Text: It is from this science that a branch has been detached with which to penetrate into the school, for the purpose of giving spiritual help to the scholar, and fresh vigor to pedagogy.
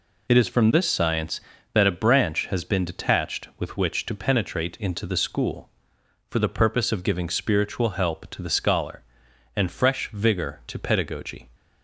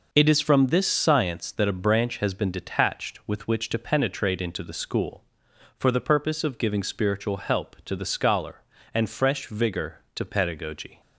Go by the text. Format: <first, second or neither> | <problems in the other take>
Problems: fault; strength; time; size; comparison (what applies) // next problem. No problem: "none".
neither | none